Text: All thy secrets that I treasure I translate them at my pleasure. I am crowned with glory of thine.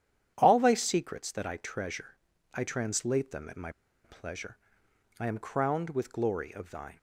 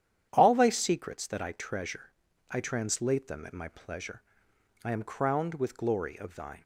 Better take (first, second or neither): second